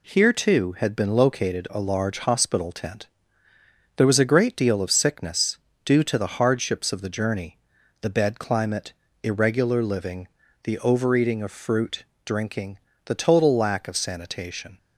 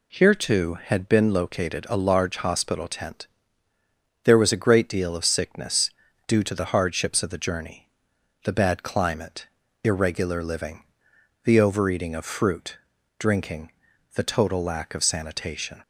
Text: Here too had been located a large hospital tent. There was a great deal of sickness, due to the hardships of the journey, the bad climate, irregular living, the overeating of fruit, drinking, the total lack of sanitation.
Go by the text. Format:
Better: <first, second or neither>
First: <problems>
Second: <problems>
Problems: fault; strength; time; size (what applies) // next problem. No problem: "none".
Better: second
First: says "bed" for "bad"; at 8.0 s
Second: none